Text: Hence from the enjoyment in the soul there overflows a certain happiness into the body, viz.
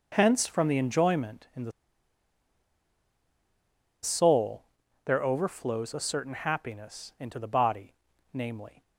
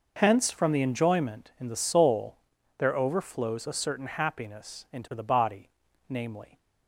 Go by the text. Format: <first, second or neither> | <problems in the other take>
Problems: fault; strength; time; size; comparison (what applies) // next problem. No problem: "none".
second | pauses between "the" and "soul"; strong; at 1.7 s; 2.3 s long // pauses between "soul" and "there"; at 4.6 s; 0.42 s long; also in the second